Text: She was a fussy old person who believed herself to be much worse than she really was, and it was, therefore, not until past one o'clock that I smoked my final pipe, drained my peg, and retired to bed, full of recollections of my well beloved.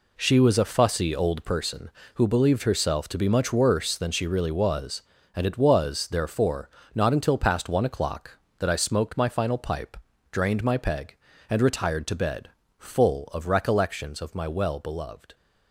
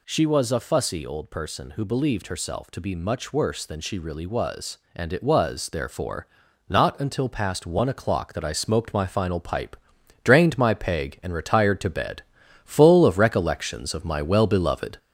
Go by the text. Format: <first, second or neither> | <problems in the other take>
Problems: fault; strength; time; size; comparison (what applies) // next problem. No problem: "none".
first | gets louder; noticeable; throughout; 4 dB